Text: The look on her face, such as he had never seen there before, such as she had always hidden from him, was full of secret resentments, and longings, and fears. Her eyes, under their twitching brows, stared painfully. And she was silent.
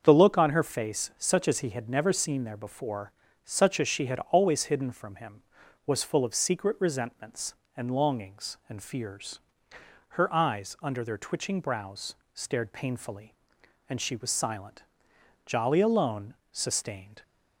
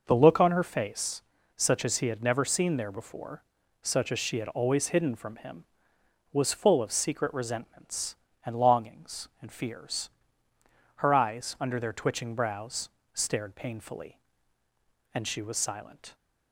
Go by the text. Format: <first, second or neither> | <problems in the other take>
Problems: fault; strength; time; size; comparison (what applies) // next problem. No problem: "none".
second | starts louder than the rest; until 1.0 s; 6.5 dB // goes on to say "Jolly alone sustained"; strong; from 15.4 s on; 1.7 s long